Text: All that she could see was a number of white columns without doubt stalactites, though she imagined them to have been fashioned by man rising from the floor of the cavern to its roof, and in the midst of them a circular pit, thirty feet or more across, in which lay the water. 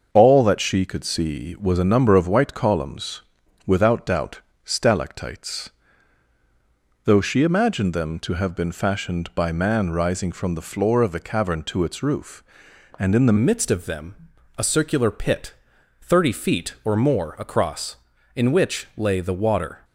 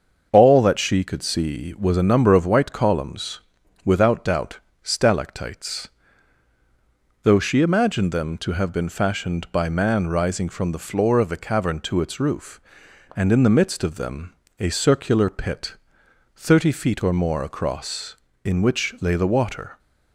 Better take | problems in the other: second | starts louder than the rest; until 1.1 s; 6.5 dB; also in the second // pauses between "columns" and "without"; at 3.2 s; 0.44 s long; also in the second // pauses between "doubt" and "stalactites"; slight; at 4.4 s; 0.24 s long; slight in the second // changes voice at "midst"; from 13.3 s on; 6.5 s long // pauses between "them" and "a"; at 14.1 s; 0.42 s long; slight in the second

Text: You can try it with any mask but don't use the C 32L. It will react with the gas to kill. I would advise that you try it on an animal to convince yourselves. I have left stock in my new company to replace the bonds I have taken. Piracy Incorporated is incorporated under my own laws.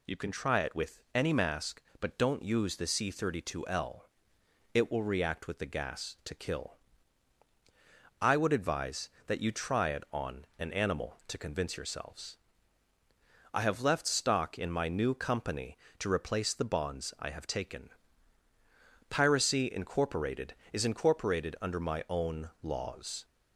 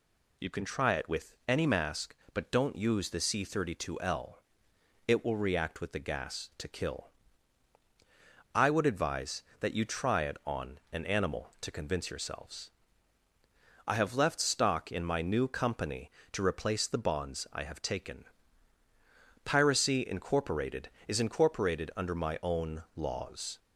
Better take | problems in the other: neither | pauses between "with" and "any"; slight; the same in both

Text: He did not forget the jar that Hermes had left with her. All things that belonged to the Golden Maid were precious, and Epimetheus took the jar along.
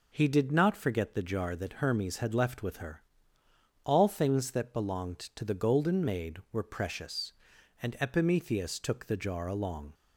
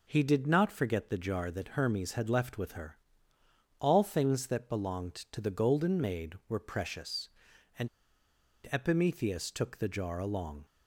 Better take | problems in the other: first | pauses between "and" and "Epimetheus"; noticeable; at 7.8 s; 0.83 s long

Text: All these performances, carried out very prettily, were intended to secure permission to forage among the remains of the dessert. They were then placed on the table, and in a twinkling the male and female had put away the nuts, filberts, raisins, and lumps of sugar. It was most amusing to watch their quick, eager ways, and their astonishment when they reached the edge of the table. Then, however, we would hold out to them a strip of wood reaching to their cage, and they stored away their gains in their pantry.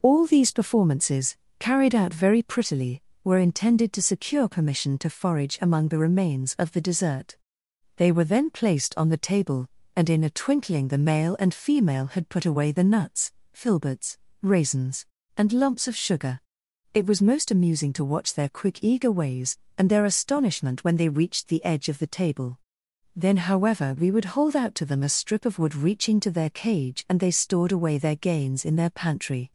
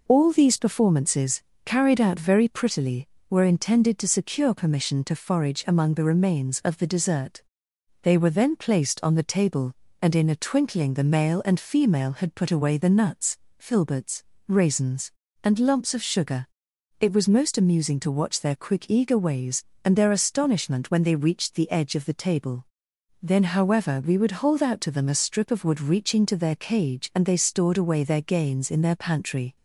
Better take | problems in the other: neither | none

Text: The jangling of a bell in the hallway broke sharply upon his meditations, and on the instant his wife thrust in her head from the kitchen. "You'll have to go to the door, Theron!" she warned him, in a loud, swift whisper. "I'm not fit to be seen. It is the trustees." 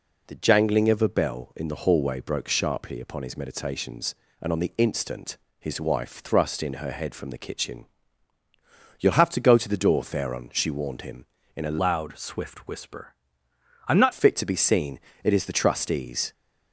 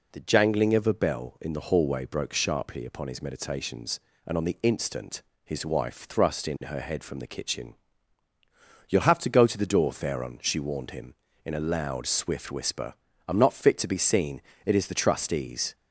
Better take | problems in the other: second | pauses between "instant" and "his"; slight; at 5.3 s; 0.24 s long; slight in the second // changes voice from "loud" to "not"; from 11.8 to 14.1 s; 2.3 s long

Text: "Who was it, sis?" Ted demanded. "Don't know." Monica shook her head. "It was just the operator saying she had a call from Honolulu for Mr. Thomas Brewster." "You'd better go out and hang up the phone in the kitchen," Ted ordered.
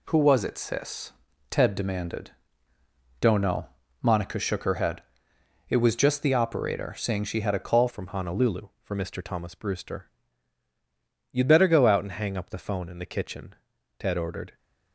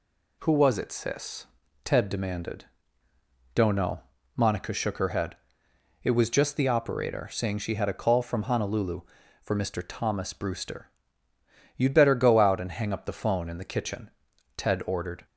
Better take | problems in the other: second | changes voice at "from"; from 7.8 s on; 6.7 s long

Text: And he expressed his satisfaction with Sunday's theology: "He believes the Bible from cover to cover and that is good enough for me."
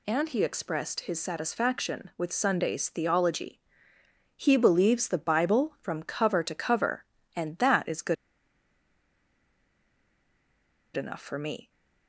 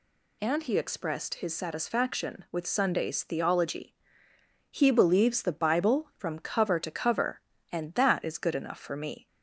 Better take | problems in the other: second | pauses between "good" and "enough"; strong; at 8.1 s; 2.8 s long

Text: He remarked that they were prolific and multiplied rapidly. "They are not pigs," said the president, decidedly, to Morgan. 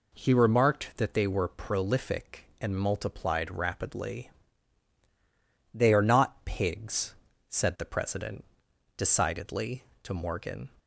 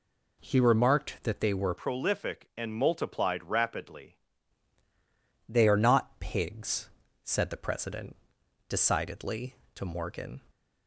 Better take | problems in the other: first | changes voice from "prolific" to "rapidly"; from 1.7 to 4.1 s; 2.4 s long

